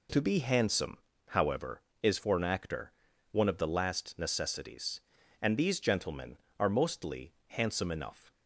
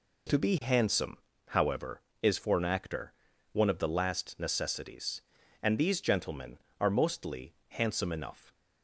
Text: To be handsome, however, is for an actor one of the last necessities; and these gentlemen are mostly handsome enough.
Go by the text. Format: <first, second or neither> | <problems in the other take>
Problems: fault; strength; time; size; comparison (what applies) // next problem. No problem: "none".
neither | pauses between "actor" and "one"; the same in both